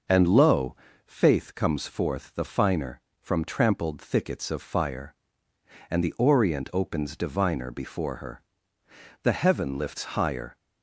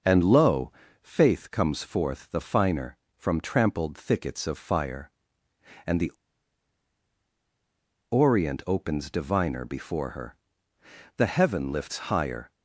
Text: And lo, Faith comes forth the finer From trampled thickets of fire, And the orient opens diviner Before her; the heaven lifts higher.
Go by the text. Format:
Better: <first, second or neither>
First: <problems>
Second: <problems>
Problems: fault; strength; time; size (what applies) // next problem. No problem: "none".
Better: first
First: none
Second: pauses between "the" and "orient"; strong; at 6.1 s; 2.0 s long